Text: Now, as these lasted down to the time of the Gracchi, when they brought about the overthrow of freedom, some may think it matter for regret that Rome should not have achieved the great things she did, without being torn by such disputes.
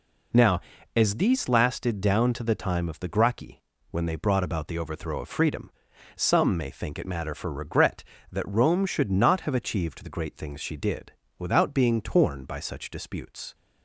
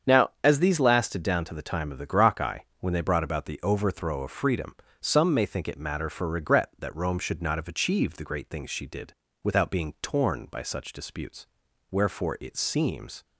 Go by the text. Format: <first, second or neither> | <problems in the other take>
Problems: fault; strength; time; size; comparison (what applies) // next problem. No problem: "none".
first | starts louder than the rest; strong; until 1.1 s; 7.5 dB // goes on to say "Wherefore it seems"; from 11.9 s on; 1.3 s long